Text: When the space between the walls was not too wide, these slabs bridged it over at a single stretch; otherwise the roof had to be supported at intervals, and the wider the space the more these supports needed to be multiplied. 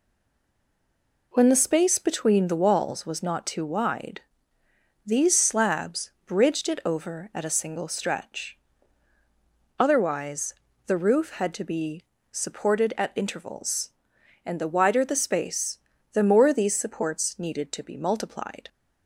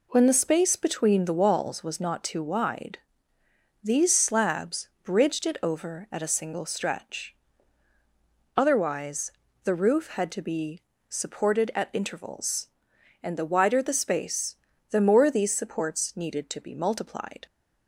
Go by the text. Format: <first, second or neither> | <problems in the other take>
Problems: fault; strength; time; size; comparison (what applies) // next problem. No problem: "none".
second | stays silent before the first word; noticeable; until 1.3 s; 1.3 s long // pauses between "slabs" and "bridged"; slight; at 6.1 s; 0.16 s long; slight in the second // pauses between "otherwise" and "the"; slight; at 10.5 s; 0.36 s long; slight in the second // pauses between "be" and "supported"; slight; at 12.0 s; 0.30 s long; slight in the second // pauses between "space" and "the"; slight; at 15.7 s; 0.34 s long; slight in the second